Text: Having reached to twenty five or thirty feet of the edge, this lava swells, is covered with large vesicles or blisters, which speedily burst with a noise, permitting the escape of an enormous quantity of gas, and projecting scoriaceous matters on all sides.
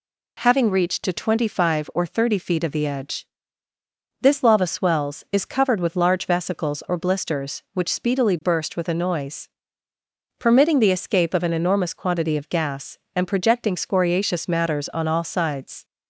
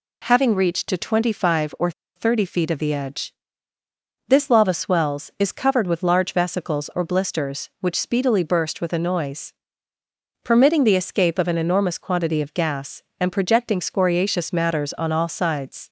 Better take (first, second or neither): first